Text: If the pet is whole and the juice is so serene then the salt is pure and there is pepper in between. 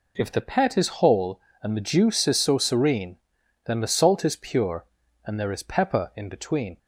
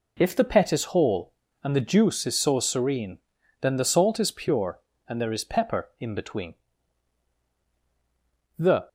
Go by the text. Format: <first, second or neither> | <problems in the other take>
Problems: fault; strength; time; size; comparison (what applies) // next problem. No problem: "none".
first | pauses between "serene" and "then"; at 3.1 s; 0.42 s long; noticeable in the first // goes on to say "The"; slight; from 8.5 s on; 0.30 s long